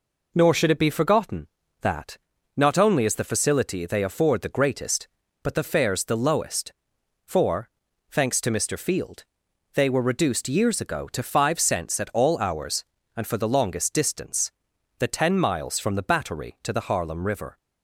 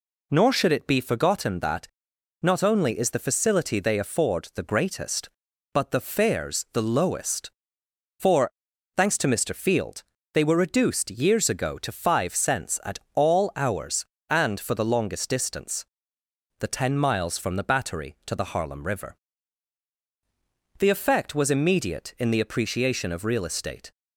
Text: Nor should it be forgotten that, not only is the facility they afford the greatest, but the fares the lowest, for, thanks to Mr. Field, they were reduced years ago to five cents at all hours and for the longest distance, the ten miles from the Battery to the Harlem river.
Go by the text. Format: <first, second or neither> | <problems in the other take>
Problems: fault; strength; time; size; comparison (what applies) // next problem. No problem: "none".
first | pauses between "at" and "all"; slight; at 12.9 s; 0.16 s long // goes on to say "The effect was immediate in the appreciation of real estate"; strong; from 20.7 s on; 3.1 s long